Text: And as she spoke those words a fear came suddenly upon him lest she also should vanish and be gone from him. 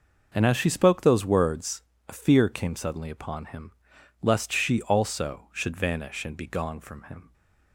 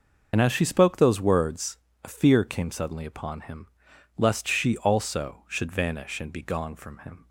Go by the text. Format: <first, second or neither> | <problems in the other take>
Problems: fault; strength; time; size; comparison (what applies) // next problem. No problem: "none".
first | loses the start of "And"; at 0.3 s; 50 ms // pauses between "words" and "a"; slight; at 1.7 s; 0.26 s long; slight in the first // pauses between "him" and "lest"; noticeable; at 3.6 s; 0.50 s long; noticeable in the first